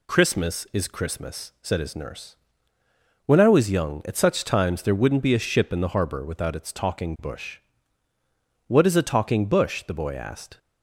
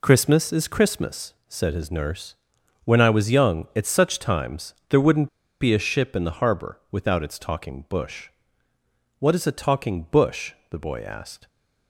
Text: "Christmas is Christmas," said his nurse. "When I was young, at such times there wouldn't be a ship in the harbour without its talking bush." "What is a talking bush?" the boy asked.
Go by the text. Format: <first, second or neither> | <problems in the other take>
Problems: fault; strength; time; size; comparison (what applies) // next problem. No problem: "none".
first | pauses between "times" and "there"; slight; at 4.7 s; 0.16 s long // pauses between "wouldn't" and "be"; slight; at 5.2 s; 0.32 s long